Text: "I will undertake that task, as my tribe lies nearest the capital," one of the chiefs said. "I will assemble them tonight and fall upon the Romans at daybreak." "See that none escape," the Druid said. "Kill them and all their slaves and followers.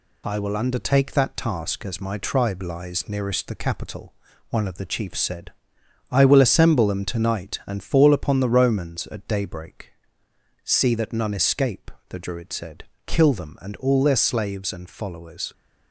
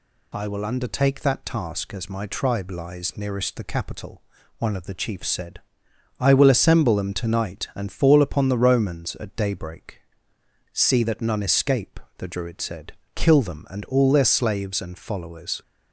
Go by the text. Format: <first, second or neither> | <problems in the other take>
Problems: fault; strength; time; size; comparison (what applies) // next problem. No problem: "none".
second | gets quieter; slight; throughout; 2.5 dB